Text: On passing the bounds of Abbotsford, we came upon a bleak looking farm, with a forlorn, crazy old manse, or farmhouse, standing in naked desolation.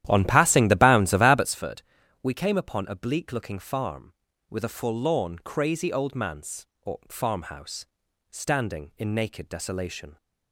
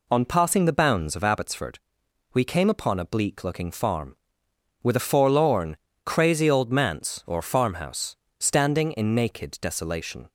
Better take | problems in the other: second | starts louder than the rest; strong; until 1.6 s; 12 dB

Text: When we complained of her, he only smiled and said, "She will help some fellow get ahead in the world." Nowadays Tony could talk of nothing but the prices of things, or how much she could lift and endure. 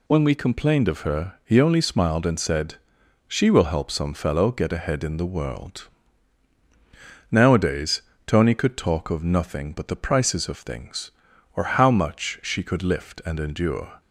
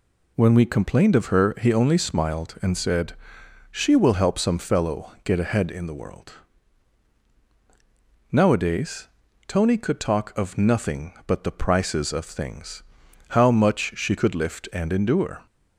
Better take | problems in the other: first | pauses between "Nowadays" and "Tony"; at 9.0 s; 0.40 s long; slight in the first // skips "or"; at 13.0 s

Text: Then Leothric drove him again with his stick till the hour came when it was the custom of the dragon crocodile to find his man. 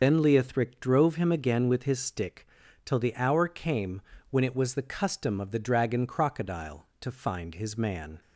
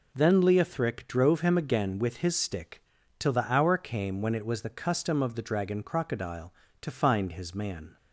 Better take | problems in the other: second | loses the start of "Then"; at 0.0 s; 55 ms // pauses between "stick" and "till"; at 2.4 s; 0.38 s long; slight in the second // pauses between "came" and "when"; slight; at 4.0 s; 0.28 s long

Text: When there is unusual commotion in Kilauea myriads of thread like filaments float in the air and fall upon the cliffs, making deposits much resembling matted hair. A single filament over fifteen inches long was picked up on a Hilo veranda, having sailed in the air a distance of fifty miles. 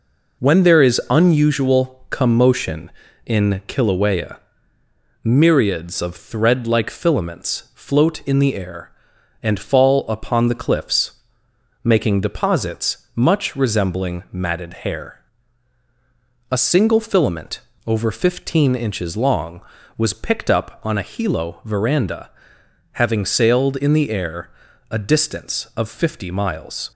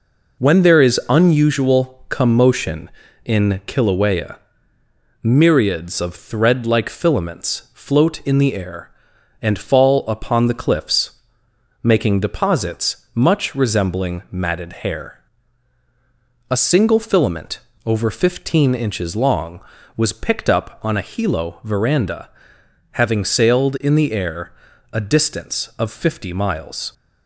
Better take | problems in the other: neither | pauses between "Kilauea" and "myriads"; noticeable; the same in both // pauses between "matted" and "hair"; slight; the same in both // pauses between "filament" and "over"; slight; the same in both // pauses between "air" and "a"; the same in both

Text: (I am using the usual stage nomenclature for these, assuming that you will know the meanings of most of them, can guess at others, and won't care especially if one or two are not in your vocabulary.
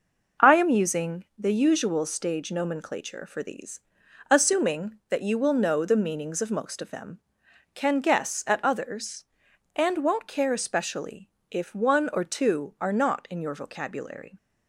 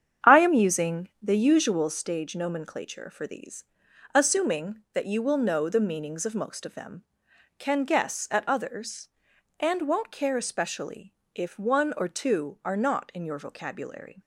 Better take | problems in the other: first | starts louder than the rest; strong; until 2.0 s; 8.5 dB // pauses between "especially" and "if"; slight; at 11.1 s; 0.20 s long; slight in the first

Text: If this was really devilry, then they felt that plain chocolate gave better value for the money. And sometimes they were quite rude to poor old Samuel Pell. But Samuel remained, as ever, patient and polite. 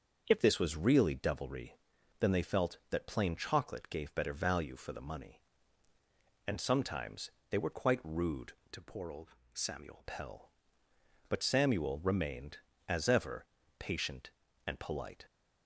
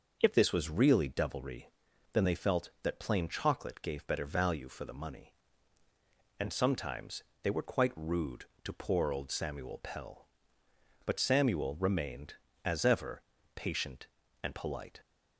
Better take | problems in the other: second | starts louder than the rest; until 1.2 s; 6.5 dB // pauses between "sometimes" and "they"; slight; at 7.2 s; 0.22 s long; slight in the second // changes voice from "to" to "Samuel"; from 8.7 to 10.0 s; 1.3 s long // pauses between "old" and "Samuel"; slight; at 9.2 s; 0.24 s long

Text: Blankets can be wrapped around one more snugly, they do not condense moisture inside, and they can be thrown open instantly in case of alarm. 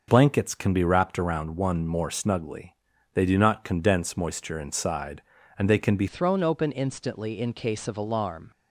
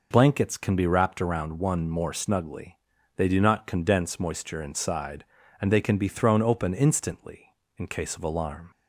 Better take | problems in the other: second | changes voice at "thrown"; from 6.0 s on; 2.5 s long

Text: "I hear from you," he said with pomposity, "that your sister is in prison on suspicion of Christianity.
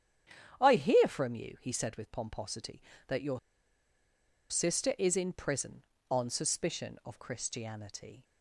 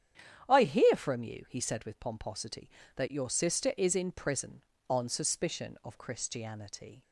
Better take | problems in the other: second | starts louder than the rest; strong; until 1.6 s; 10 dB; strong in the second // pauses between "your" and "sister"; at 3.3 s; 1.1 s long

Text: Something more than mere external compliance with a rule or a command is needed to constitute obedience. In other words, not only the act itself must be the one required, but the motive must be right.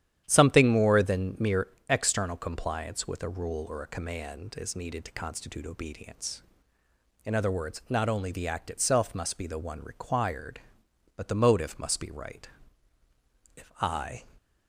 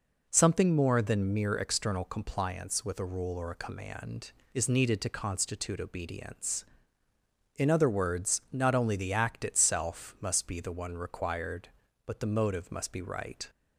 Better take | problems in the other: second | starts louder than the rest; strong; until 1.2 s; 10.5 dB // pauses between "mere" and "external"; slight; at 1.6 s; 0.22 s long // goes on to say "If I"; noticeable; from 13.5 s on; 0.68 s long

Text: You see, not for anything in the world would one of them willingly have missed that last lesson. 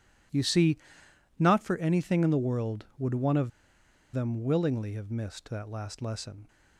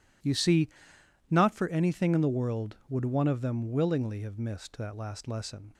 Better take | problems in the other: second | pauses between "of" and "them"; noticeable; at 3.5 s; 0.63 s long

